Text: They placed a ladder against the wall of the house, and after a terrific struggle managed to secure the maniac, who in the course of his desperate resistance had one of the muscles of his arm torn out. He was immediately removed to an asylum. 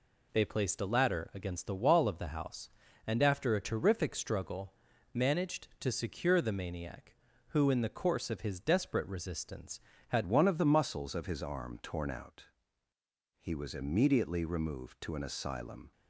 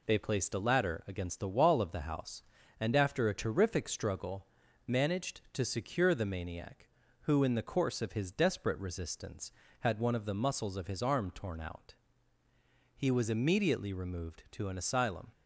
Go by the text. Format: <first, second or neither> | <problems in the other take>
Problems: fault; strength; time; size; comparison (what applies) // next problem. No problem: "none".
second | pauses between "struggle" and "managed"; at 4.7 s; 0.40 s long; also in the second // changes voice at "one"; from 10.2 s on; 5.7 s long